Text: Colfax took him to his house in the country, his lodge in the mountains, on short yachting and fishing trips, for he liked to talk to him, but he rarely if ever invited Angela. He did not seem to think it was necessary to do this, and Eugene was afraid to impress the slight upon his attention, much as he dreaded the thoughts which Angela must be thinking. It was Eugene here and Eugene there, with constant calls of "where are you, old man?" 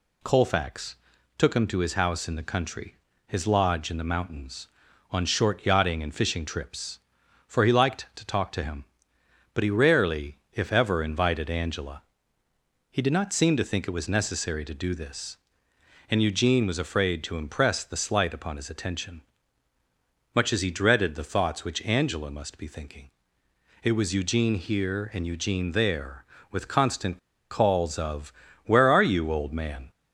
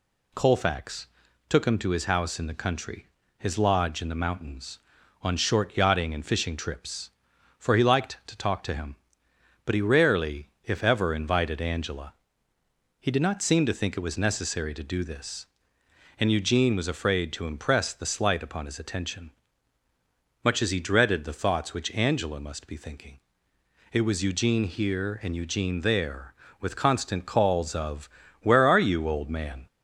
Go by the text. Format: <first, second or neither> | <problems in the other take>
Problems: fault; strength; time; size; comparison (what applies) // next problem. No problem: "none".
second | pauses between "Colfax" and "took"; at 0.9 s; 0.42 s long; also in the second // pauses between "constant" and "calls"; slight; at 27.1 s; 0.33 s long // pauses between "of" and "where"; slight; at 28.3 s; 0.32 s long; slight in the second